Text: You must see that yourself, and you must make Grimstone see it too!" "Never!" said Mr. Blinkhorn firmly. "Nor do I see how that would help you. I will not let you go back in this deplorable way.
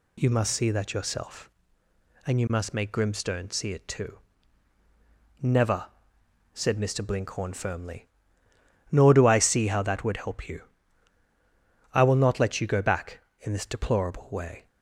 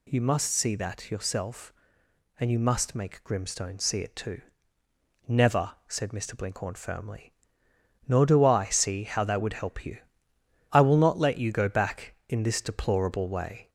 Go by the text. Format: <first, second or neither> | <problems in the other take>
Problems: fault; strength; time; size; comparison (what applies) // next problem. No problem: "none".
first | gets louder; slight; throughout; 2 dB